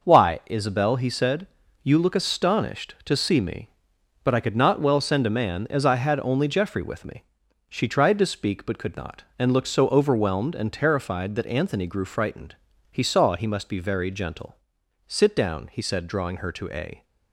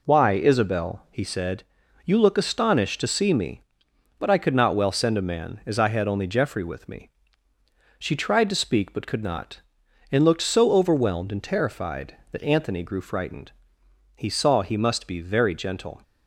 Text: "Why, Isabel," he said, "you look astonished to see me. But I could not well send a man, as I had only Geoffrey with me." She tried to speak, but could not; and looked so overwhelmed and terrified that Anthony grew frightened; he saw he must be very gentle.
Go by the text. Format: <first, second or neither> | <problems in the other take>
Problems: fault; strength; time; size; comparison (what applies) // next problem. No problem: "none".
second | goes on to say "Sit down he said drawing her to a"; strong; from 15.0 s on; 1.9 s long